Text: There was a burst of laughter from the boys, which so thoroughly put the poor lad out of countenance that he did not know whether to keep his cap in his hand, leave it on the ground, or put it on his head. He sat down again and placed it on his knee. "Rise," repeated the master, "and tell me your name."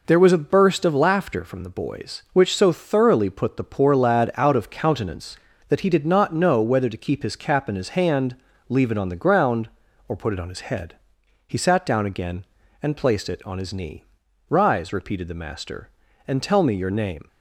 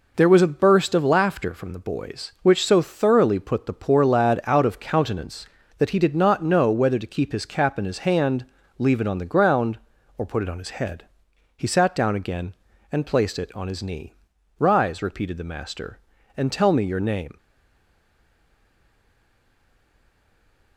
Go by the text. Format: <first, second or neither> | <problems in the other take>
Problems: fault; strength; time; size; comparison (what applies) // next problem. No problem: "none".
first | stays silent after the last word; strong; from 17.3 s on; 3.4 s long